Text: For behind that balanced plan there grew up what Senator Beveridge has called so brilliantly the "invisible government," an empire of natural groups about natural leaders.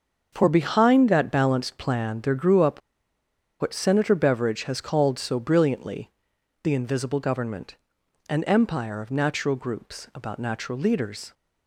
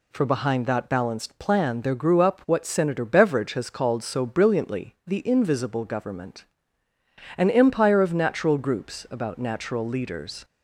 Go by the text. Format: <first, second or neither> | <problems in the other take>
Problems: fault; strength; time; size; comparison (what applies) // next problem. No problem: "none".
second | starts louder than the rest; until 1.3 s; 6.5 dB // pauses between "up" and "what"; noticeable; at 2.8 s; 0.80 s long // pauses between "brilliantly" and "the"; noticeable; at 6.0 s; 0.54 s long